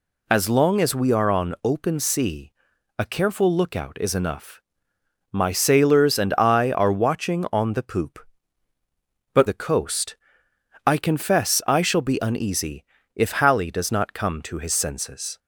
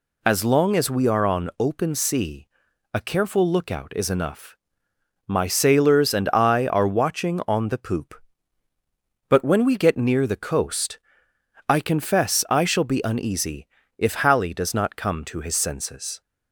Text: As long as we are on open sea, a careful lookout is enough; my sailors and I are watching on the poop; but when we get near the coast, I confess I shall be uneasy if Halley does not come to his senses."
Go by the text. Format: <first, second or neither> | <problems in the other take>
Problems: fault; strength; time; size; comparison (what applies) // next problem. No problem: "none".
second | skips "when we get near"; at 9.4 s // pauses between "uneasy" and "if"; slight; at 12.8 s; 0.32 s long; slight in the second